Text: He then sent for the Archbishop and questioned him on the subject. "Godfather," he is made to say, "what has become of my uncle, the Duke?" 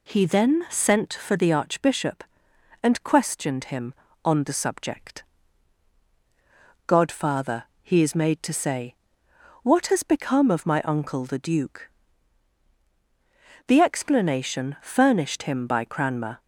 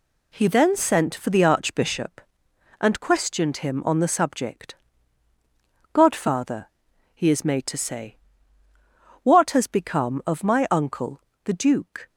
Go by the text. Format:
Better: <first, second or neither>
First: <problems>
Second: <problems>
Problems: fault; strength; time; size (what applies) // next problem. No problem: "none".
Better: second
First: goes on to say "The explanation furnished him by Cranmer"; strong; from 13.6 s on; 2.7 s long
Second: none